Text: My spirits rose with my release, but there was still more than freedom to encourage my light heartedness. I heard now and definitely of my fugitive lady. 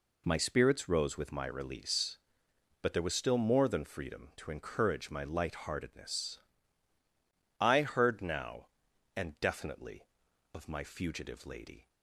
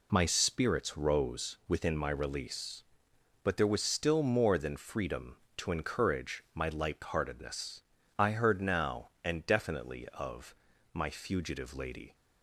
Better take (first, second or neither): first